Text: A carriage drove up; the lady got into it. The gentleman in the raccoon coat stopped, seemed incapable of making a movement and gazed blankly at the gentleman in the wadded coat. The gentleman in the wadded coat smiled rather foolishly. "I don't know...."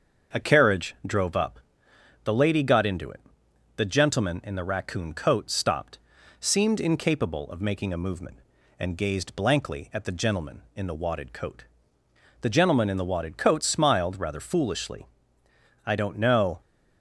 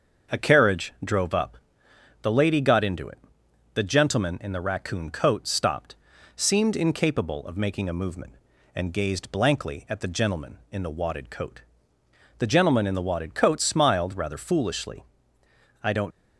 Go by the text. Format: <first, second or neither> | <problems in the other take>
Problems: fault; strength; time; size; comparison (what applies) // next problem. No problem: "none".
first | starts louder than the rest; until 1.4 s; 6.5 dB; also in the first // stops before "know"; at 16.1 s